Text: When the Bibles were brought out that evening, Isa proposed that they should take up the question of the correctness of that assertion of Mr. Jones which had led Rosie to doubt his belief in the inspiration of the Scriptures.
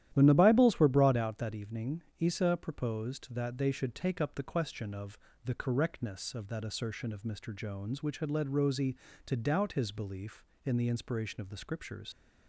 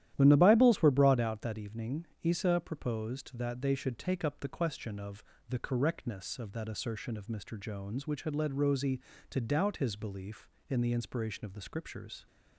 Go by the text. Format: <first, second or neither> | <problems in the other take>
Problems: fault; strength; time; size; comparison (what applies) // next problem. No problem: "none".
second | starts louder than the rest; strong; until 1.1 s; 12 dB; strong in the second // pauses between "of" and "the"; slight; at 5.1 s; 0.28 s long; slight in the second // leaves "Scriptures" unfinished; at 12.1 s; 100 ms